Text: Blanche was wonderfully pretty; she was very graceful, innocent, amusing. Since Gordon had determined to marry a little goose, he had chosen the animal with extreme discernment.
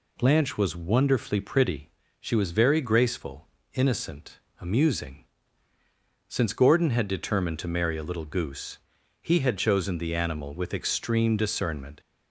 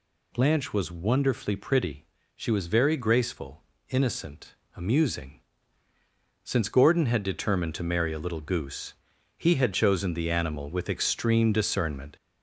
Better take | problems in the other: first | gets louder; slight; throughout; 3.5 dB

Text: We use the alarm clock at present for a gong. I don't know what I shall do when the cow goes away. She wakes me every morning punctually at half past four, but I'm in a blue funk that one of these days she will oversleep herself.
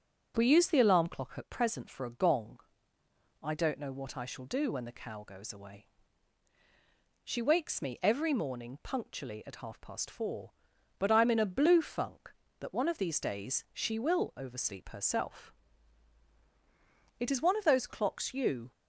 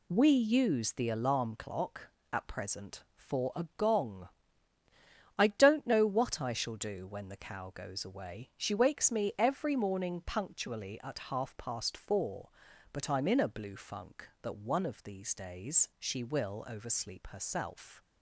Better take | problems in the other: second | goes on to say "It is one of those clocks you"; from 17.1 s on; 1.5 s long

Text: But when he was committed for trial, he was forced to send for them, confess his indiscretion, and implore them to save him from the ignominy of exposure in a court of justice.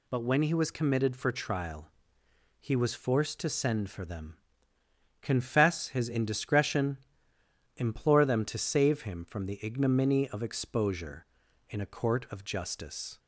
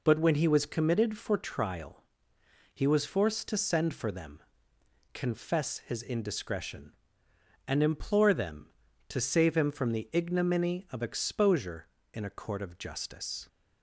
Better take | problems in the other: second | skips "and"; at 7.3 s

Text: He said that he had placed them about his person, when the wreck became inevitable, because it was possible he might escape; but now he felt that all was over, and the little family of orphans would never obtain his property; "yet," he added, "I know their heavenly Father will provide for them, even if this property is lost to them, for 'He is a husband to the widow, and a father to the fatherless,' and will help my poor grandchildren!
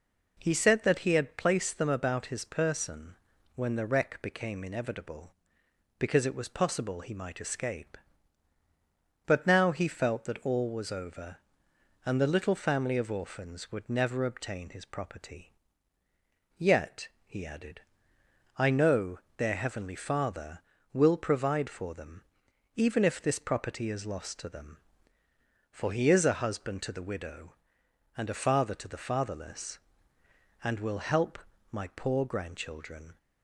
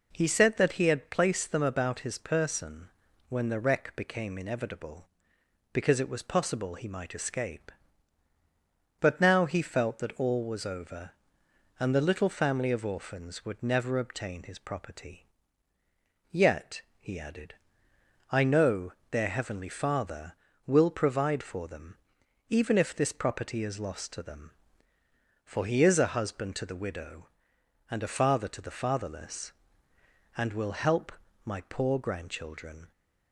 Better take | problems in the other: neither | pauses between "know" and "their"; slight; the same in both // pauses between "help" and "my"; slight; the same in both

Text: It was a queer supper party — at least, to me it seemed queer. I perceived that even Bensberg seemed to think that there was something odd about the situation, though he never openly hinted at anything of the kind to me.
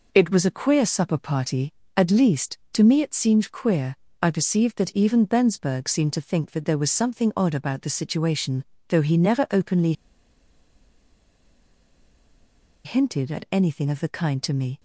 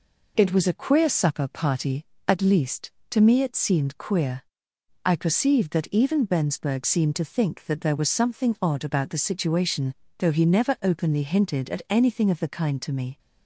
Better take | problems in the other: second | pauses between "openly" and "hinted"; strong; at 9.9 s; 2.9 s long

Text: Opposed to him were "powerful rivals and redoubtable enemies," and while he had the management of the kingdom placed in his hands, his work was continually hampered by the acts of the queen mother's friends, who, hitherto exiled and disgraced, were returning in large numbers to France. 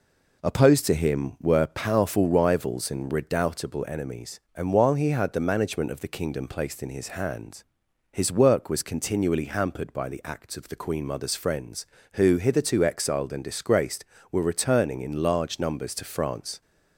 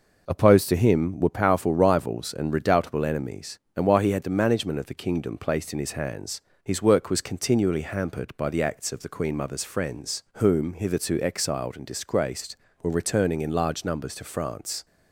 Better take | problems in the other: first | says "whom" for "who"; at 10.3 s

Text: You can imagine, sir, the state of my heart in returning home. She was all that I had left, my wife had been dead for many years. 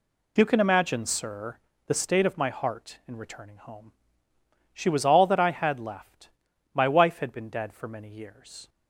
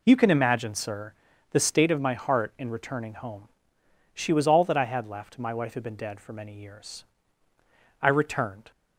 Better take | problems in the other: first | goes on to say "I returned"; noticeable; from 8.0 s on; 0.70 s long

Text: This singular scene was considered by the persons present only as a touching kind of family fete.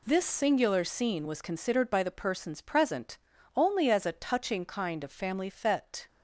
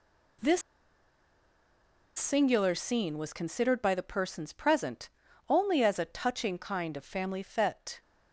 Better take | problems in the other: first | pauses between "This" and "singular"; strong; at 0.6 s; 1.5 s long // pauses between "present" and "only"; at 5.0 s; 0.40 s long; also in the first

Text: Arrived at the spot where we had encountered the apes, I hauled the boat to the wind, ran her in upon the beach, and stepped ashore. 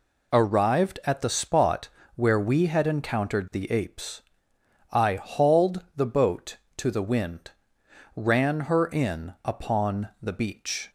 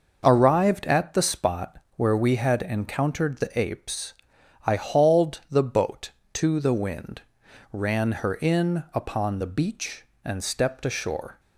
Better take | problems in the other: second | pauses between "spot" and "where"; slight; at 1.8 s; 0.26 s long; slight in the second // stops before "and stepped ashore"; at 10.8 s

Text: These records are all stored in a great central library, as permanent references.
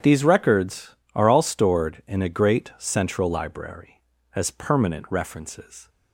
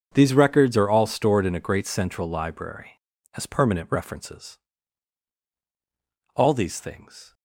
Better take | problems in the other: first | starts louder than the rest; until 1.1 s; 6.5 dB; strong in the first // goes on to say "All these things"; noticeable; from 6.3 s on; 0.98 s long

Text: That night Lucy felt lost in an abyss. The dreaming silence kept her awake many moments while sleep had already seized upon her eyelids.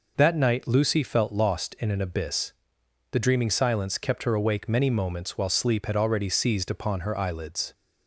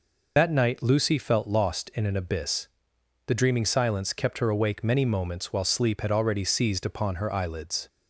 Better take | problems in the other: first | loses the start of "That"; at 0.3 s; 40 ms

